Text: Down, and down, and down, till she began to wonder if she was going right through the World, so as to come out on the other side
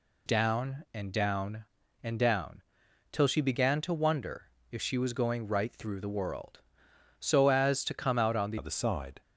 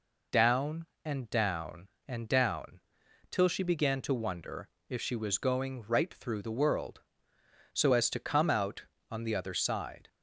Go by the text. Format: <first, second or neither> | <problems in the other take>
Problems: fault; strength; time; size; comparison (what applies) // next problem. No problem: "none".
second | pauses between "wonder" and "if"; slight; at 4.4 s; 0.22 s long; slight in the second // changes voice at "other"; from 8.5 s on; 0.7 s long